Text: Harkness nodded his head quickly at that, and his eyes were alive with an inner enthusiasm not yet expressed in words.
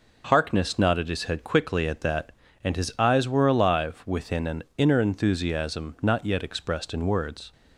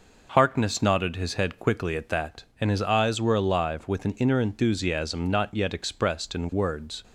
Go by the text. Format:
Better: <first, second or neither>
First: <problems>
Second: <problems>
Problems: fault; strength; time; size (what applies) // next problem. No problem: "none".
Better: second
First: says "within" for "with"; at 4.0 s // pauses between "an" and "inner"; slight; at 4.6 s; 0.16 s long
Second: none